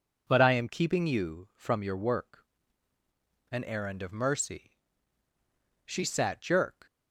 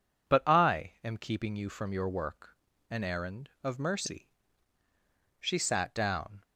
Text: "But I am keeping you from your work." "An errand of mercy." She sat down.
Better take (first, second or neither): second